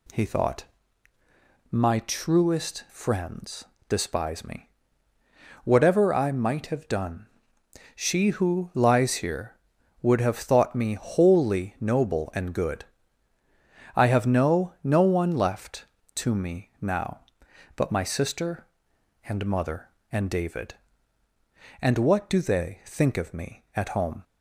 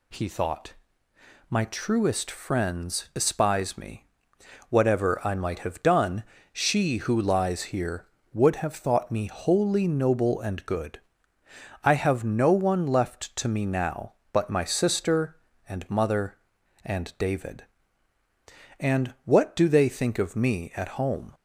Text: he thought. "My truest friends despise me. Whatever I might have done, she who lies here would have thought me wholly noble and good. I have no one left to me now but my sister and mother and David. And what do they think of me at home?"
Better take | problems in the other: second | pauses between "friends" and "despise"; slight; at 3.6 s; 0.24 s long // says "no" twice; at 14.8 s

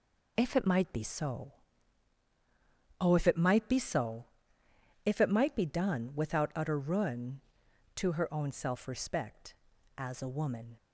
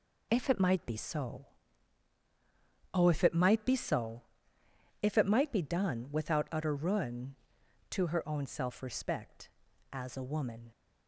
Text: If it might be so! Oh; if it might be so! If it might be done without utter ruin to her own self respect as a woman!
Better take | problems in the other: neither | none

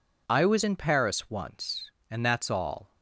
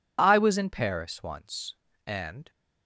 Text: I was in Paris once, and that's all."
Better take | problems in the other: first | stops before "that's all"; at 2.4 s

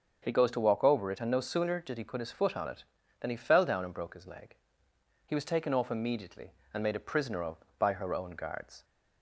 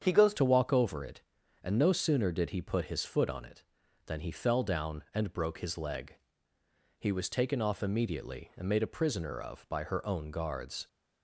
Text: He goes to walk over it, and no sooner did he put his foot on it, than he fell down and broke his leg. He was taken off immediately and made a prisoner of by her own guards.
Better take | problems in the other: first | starts louder than the rest; strong; until 1.0 s; 8 dB; also in the first // changes voice at "to"; from 0.3 s on; 10.5 s long

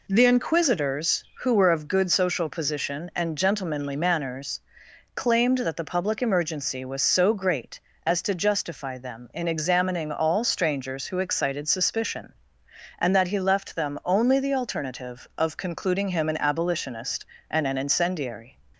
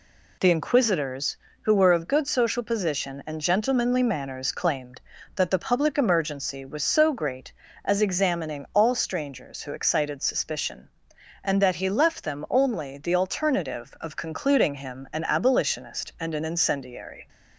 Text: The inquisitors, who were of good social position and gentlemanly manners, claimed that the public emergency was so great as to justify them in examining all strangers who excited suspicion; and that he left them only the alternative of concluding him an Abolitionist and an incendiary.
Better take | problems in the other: first | skips "to justify them in"; at 8.0 s

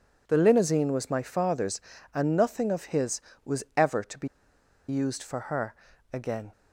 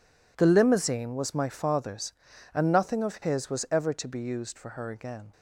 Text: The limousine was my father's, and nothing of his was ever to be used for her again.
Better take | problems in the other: second | pauses between "be" and "used"; noticeable; at 4.2 s; 0.61 s long // pauses between "her" and "again"; at 5.7 s; 0.38 s long

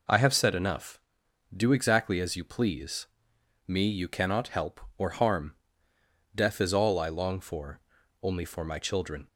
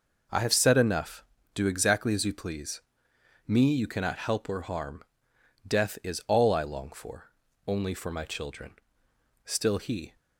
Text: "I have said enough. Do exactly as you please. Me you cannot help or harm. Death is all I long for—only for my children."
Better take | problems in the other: first | goes on to say "Still he"; noticeable; from 9.4 s on; 0.70 s long

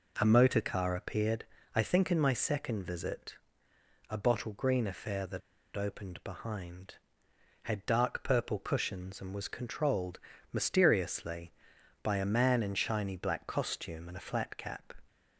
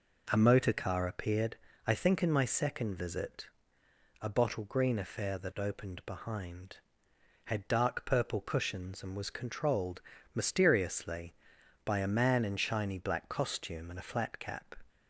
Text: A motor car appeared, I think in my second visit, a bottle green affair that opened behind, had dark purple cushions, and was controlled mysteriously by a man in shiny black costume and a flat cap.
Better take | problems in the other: second | pauses between "that" and "opened"; at 5.4 s; 0.36 s long // pauses between "controlled" and "mysteriously"; slight; at 10.1 s; 0.34 s long; slight in the second

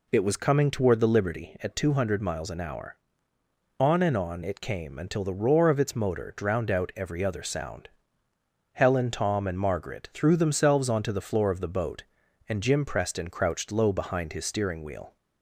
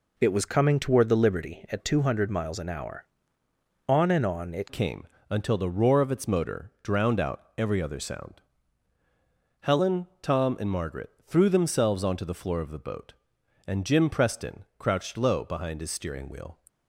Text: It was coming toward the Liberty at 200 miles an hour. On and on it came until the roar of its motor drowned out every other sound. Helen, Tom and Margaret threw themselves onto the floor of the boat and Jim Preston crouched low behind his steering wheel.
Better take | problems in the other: first | changes voice at "came"; from 4.7 s on; 11.8 s long // pauses between "came" and "until"; slight; at 5.0 s; 0.24 s long // pauses between "Margaret" and "threw"; slight; at 11.1 s; 0.16 s long

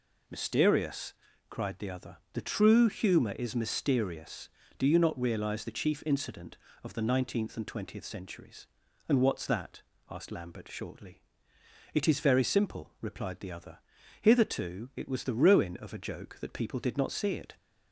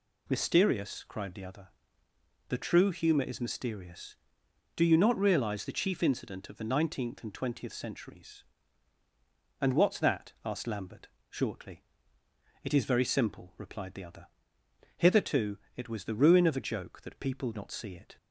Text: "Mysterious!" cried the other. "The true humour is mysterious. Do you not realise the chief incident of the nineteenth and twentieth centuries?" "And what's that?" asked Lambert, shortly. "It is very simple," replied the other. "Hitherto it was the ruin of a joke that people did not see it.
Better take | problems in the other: first | pauses between "Hitherto" and "it"; slight; at 15.5 s; 0.18 s long // skips "did"; at 17.5 s

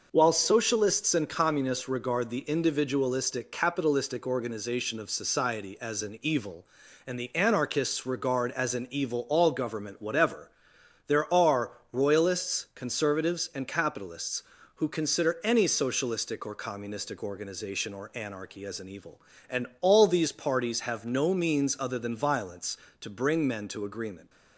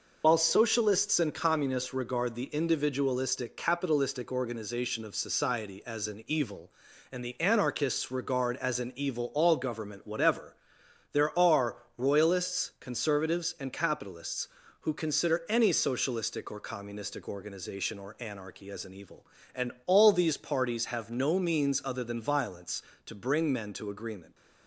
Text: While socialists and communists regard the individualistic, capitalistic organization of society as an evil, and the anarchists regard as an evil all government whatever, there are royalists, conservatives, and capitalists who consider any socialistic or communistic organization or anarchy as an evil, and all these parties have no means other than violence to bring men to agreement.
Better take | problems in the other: first | loses the start of "While"; at 0.2 s; 80 ms // pauses between "are" and "royalists"; slight; at 11.7 s; 0.20 s long; slight in the first // pauses between "and" and "all"; slight; at 19.7 s; 0.16 s long; slight in the first

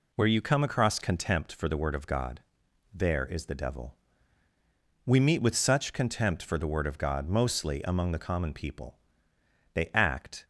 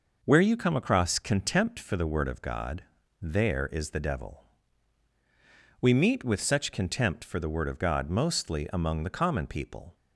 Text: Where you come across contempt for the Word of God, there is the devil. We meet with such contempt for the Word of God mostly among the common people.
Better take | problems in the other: second | goes on to say "They act"; noticeable; from 9.7 s on; 0.72 s long

